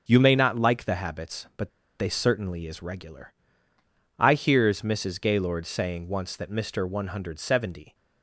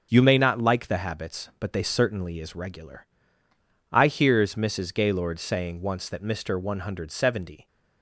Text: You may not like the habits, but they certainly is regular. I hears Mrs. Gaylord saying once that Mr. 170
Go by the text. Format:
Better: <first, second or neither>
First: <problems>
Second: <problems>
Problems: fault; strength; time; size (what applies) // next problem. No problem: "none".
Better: second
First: starts louder than the rest; until 1.0 s; 6.5 dB // pauses between "but" and "they"; slight; at 1.7 s; 0.30 s long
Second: starts louder than the rest; until 1.1 s; 6.5 dB